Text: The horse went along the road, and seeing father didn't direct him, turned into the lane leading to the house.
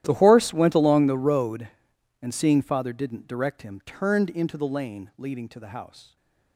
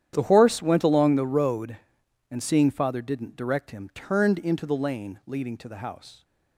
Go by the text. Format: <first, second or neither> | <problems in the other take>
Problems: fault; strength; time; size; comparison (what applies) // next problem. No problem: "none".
second | gets quieter; strong; throughout; 22 dB // starts louder than the rest; strong; until 1.0 s; 12.5 dB; strong in the second // stays silent after the last word; slight; from 6.0 s on; 0.5 s long